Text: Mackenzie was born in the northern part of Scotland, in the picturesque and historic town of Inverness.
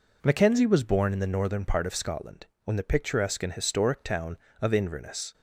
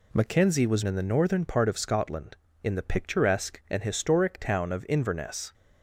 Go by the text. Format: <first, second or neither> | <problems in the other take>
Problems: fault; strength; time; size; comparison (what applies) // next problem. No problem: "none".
first | skips "born"; at 0.8 s